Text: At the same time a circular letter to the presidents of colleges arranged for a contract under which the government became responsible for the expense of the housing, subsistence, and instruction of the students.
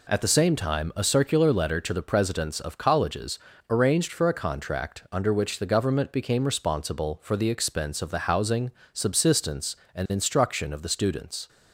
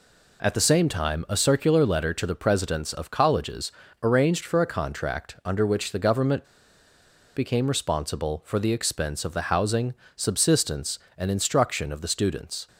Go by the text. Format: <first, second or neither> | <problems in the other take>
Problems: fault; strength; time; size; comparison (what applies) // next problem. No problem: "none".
first | pauses between "colleges" and "arranged"; slight; at 3.7 s; 0.30 s long; slight in the first // pauses between "government" and "became"; noticeable; at 6.4 s; 0.90 s long